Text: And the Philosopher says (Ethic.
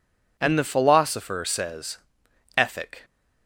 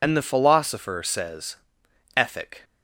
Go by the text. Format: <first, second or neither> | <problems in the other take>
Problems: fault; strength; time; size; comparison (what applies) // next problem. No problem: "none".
first | loses the start of "And"; at 0.0 s; 50 ms